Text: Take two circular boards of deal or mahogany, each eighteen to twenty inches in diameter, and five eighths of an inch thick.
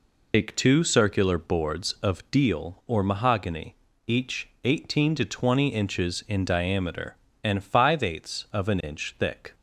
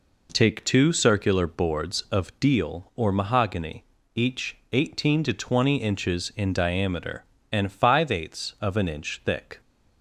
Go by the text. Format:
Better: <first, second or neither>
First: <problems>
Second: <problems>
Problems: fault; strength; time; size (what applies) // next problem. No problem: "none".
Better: second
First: loses the start of "Take"; at 0.3 s; 135 ms // pauses between "each" and "eighteen"; slight; at 4.4 s; 0.16 s long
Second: pauses between "each" and "eighteen"; slight; at 4.5 s; 0.16 s long